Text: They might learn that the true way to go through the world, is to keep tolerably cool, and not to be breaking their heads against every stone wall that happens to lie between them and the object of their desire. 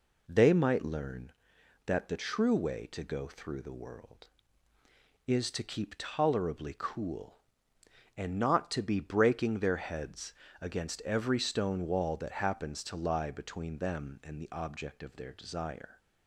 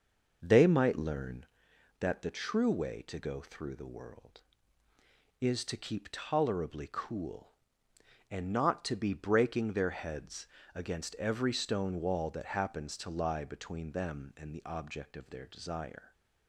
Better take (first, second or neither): first